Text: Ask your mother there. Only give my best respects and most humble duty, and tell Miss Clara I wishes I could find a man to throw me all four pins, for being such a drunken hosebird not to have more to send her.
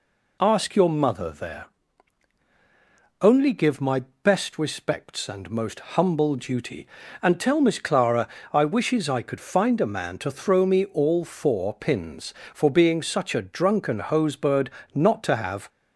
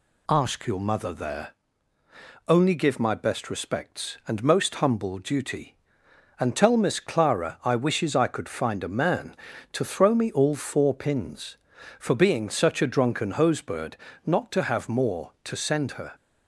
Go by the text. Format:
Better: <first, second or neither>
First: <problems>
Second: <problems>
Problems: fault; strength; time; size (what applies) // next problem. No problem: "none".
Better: second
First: pauses between "my" and "best"; slight; at 4.0 s; 0.24 s long // pauses between "most" and "humble"; slight; at 5.7 s; 0.16 s long // pauses between "Clara" and "I"; slight; at 8.2 s; 0.26 s long // pauses between "hosebird" and "not"; slight; at 14.7 s; 0.24 s long // stops before "more to send her"; at 15.6 s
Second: pauses between "hosebird" and "not"; slight; at 13.9 s; 0.30 s long